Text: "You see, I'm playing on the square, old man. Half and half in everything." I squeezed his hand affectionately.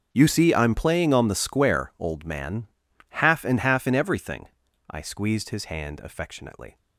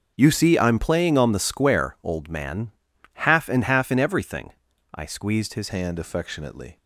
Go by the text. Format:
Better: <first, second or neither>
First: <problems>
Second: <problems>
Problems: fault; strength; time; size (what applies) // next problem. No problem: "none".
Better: first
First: starts louder than the rest; until 1.1 s; 6.5 dB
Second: starts louder than the rest; noticeable; until 1.1 s; 6 dB // changes voice at "hand"; from 5.6 s on; 1.1 s long